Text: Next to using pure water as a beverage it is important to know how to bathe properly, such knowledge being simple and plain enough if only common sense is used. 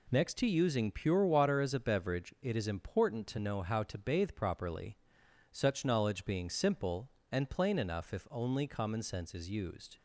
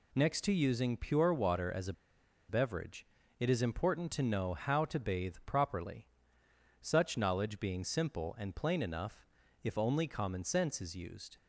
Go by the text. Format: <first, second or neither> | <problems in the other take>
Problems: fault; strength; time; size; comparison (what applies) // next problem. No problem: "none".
first | pauses between "a" and "beverage"; noticeable; at 1.9 s; 0.56 s long // pauses between "beverage" and "it"; slight; at 3.0 s; 0.34 s long // pauses between "enough" and "if"; slight; at 9.2 s; 0.36 s long